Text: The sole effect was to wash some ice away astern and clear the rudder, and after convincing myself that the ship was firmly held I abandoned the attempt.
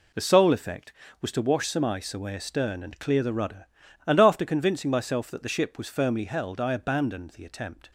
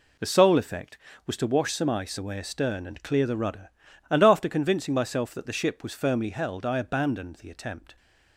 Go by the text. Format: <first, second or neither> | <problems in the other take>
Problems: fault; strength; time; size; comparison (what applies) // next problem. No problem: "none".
neither | none